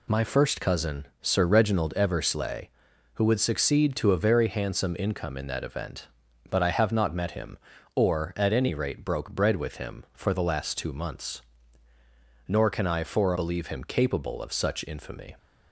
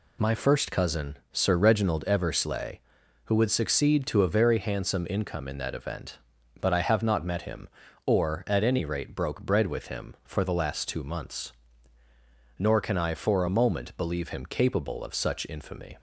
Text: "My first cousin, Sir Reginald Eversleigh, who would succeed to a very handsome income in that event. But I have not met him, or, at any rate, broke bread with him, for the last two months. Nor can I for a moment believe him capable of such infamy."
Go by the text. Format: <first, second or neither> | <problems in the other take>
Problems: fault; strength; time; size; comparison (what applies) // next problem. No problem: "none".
second | skips "a moment"; at 13.3 s